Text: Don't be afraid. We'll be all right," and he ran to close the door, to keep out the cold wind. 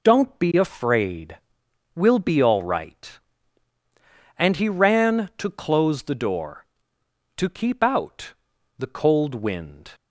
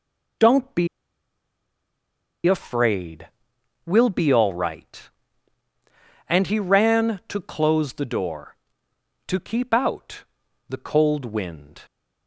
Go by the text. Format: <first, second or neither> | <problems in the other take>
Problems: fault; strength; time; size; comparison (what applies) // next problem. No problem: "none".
first | pauses between "be" and "afraid"; strong; at 0.8 s; 1.5 s long // pauses between "out" and "the"; noticeable; at 10.2 s; 0.46 s long; noticeable in the first